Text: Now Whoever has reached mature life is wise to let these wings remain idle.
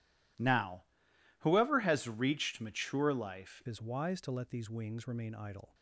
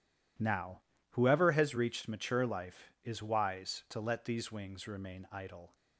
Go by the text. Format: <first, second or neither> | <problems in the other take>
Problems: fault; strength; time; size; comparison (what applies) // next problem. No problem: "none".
second | pauses between "Now" and "Whoever"; noticeable; at 0.8 s; 0.58 s long; slight in the second // changes voice at "is"; from 3.6 s on; 2.1 s long